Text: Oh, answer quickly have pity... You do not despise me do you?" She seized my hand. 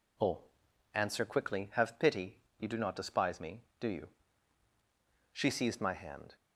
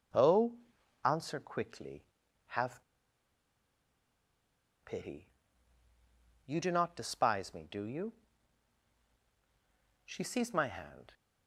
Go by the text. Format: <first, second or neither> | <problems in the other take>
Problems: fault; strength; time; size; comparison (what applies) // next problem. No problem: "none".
first | pauses between "have" and "pity"; strong; at 2.8 s; 2.0 s long